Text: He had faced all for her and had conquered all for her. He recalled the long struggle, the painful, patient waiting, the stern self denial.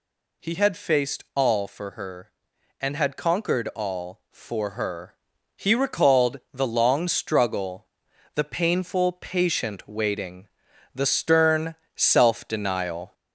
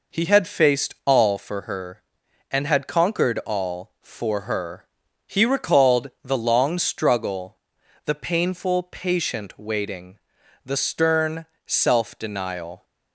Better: second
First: gets louder; slight; throughout; 2.5 dB // pauses between "stern" and "self"; slight; at 11.7 s; 0.20 s long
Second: pauses between "stern" and "self"; slight; at 11.4 s; 0.20 s long

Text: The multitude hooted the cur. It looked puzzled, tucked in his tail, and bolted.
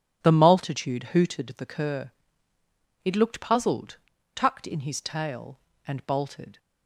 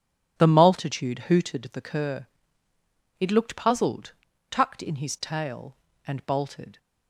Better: neither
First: none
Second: none

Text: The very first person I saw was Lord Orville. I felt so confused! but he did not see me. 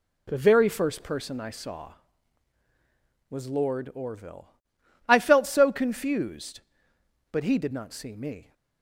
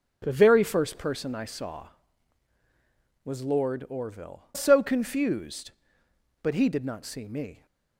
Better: first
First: none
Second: starts louder than the rest; strong; until 1.2 s; 9.5 dB // skips "I felt"; at 4.5 s

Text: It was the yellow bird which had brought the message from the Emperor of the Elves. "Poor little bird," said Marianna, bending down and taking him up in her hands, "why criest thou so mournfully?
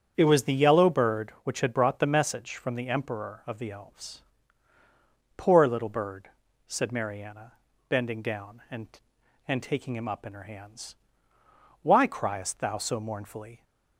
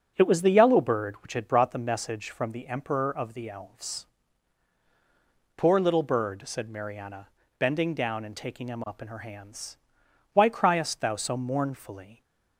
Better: second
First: starts louder than the rest; strong; until 1.1 s; 8 dB // says "and" twice; at 9.4 s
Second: starts louder than the rest; until 1.1 s; 6.5 dB

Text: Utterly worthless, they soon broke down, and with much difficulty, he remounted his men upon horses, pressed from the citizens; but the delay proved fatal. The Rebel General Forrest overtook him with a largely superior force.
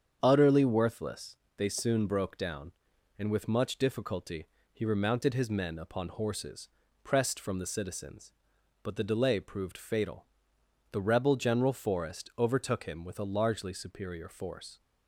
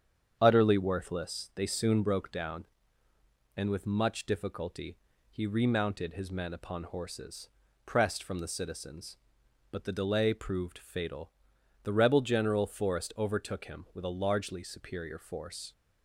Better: neither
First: starts louder than the rest; strong; until 1.2 s; 8 dB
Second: starts louder than the rest; strong; until 1.4 s; 8 dB

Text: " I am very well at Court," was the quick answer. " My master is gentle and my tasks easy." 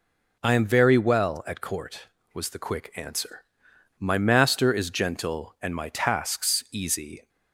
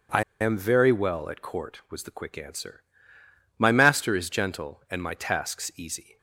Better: first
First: none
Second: pauses between "I" and "am"; slight; at 0.2 s; 0.18 s long

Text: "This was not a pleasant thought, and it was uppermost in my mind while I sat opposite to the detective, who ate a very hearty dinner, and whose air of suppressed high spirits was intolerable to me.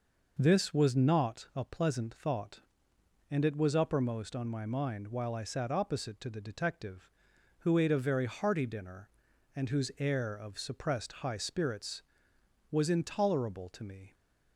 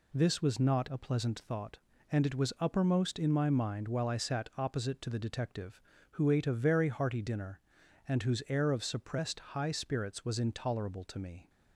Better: second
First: says "on" for "in"; at 4.3 s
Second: none

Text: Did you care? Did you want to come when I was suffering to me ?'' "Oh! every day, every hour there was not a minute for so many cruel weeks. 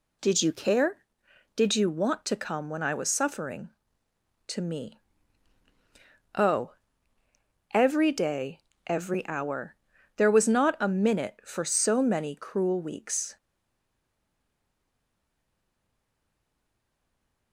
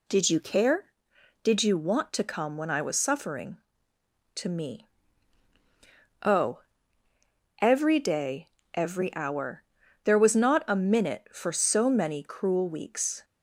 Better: second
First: pauses between "hour" and "there"; at 9.7 s; 0.40 s long // stays silent after the last word; strong; from 13.3 s on; 4.2 s long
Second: pauses between "hour" and "there"; at 9.6 s; 0.40 s long

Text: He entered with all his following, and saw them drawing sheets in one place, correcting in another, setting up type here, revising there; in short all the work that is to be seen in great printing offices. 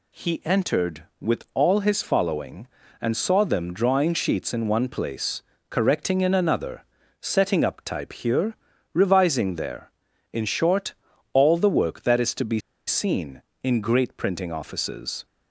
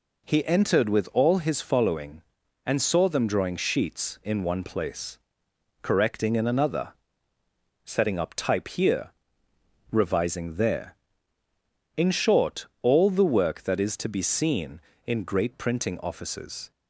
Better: second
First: pauses between "short" and "all"; at 10.9 s; 0.40 s long // pauses between "be" and "seen"; slight; at 12.5 s; 0.28 s long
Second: pauses between "short" and "all"; slight; at 12.6 s; 0.16 s long

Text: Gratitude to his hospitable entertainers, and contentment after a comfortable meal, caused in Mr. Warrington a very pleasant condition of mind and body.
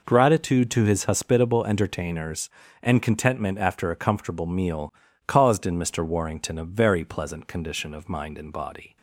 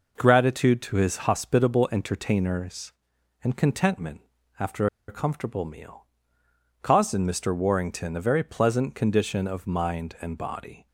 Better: first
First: none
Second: pauses between "contentment" and "after"; slight; at 4.2 s; 0.36 s long // pauses between "after" and "a"; slight; at 4.8 s; 0.20 s long

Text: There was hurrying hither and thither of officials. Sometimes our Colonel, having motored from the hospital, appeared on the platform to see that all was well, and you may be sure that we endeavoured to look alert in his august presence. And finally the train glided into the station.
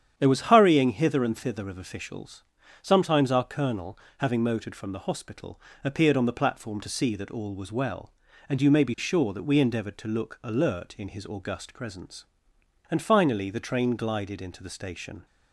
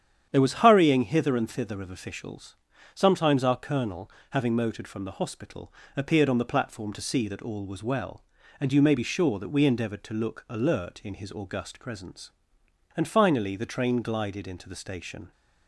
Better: neither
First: starts louder than the rest; strong; until 1.1 s; 9 dB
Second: starts louder than the rest; strong; until 1.3 s; 9 dB

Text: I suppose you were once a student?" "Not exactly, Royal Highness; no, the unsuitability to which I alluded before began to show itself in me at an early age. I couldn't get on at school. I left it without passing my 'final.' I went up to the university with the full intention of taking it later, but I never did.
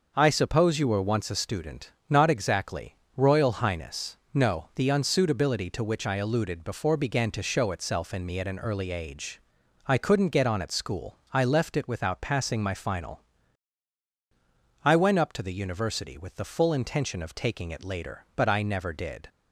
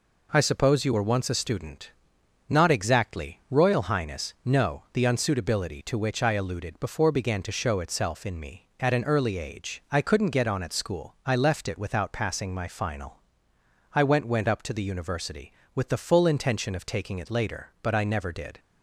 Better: first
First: none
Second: says "went" twice; at 14.2 s

